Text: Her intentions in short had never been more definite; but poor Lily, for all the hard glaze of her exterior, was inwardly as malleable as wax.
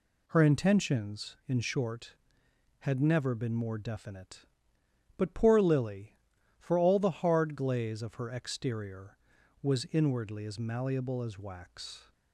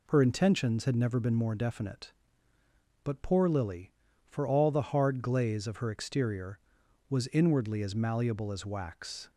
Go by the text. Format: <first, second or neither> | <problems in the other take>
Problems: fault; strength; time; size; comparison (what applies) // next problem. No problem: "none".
first | skips "in short"; at 0.8 s